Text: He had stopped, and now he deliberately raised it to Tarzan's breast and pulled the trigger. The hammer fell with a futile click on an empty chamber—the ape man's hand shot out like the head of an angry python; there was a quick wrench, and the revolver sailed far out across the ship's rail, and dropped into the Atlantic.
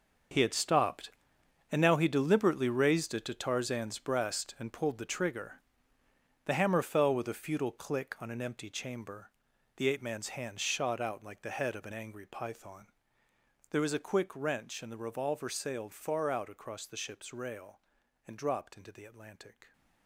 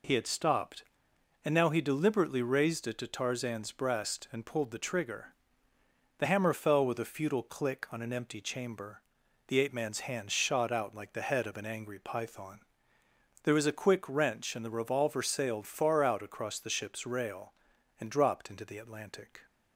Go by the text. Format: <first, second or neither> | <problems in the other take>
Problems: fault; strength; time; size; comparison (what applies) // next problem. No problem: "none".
second | gets quieter; strong; throughout; 13.5 dB